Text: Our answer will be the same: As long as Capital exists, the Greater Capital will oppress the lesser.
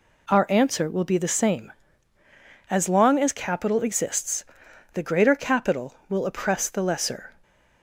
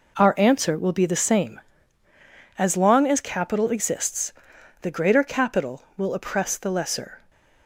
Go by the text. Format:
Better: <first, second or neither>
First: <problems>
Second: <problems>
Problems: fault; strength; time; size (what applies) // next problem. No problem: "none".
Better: first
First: none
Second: gets quieter; strong; throughout; 8.5 dB